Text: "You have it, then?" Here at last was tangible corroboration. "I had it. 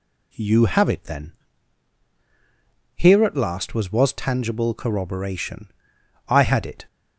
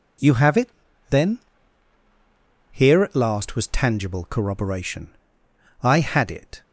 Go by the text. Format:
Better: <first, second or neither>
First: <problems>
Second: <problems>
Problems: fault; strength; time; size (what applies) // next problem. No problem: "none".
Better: second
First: says "was" twice; at 3.9 s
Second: none